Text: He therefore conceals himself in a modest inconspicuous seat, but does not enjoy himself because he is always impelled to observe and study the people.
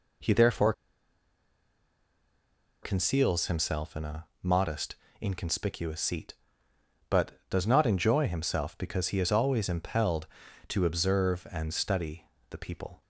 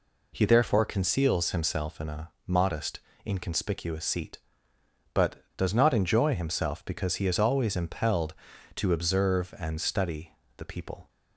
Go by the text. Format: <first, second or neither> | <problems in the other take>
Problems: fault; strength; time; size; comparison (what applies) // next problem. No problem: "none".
second | pauses between "therefore" and "conceals"; strong; at 0.7 s; 2.1 s long // pauses between "a" and "modest"; slight; at 4.2 s; 0.18 s long; slight in the second // pauses between "modest" and "inconspicuous"; slight; at 4.9 s; 0.26 s long; slight in the second // pauses between "study" and "the"; slight; at 12.2 s; 0.22 s long; slight in the second